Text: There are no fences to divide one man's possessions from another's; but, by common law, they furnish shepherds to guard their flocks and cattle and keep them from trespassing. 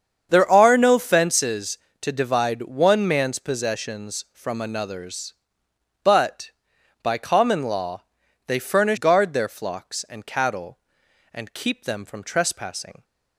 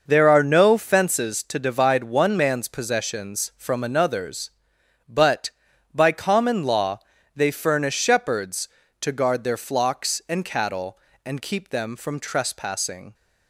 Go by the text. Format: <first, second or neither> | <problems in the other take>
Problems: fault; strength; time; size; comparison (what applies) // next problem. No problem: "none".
second | starts louder than the rest; strong; until 1.3 s; 7.5 dB // skips "shepherds to"; at 8.9 s